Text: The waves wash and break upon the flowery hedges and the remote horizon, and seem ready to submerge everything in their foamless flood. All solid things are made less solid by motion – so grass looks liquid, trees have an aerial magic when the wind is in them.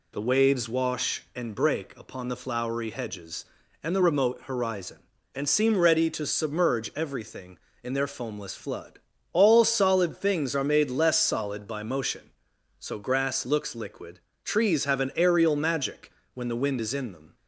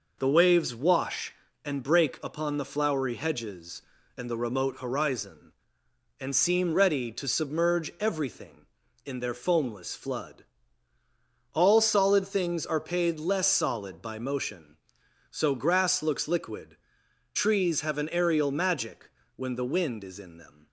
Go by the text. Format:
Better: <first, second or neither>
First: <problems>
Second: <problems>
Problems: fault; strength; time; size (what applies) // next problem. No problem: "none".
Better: first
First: pauses between "magic" and "when"; slight; at 16.1 s; 0.22 s long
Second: says "paid" for "made"; at 12.7 s // pauses between "magic" and "when"; slight; at 19.0 s; 0.26 s long